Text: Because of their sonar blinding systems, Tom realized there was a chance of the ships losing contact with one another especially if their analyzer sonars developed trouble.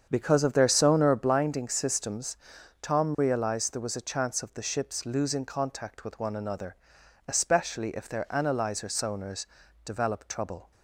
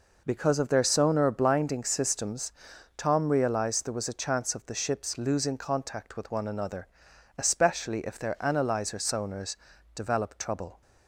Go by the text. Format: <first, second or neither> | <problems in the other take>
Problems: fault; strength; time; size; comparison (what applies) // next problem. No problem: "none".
second | starts louder than the rest; strong; until 1.2 s; 7.5 dB // pauses between "another" and "especially"; noticeable; at 6.7 s; 0.52 s long; noticeable in the second // pauses between "sonars" and "developed"; at 9.4 s; 0.40 s long; also in the second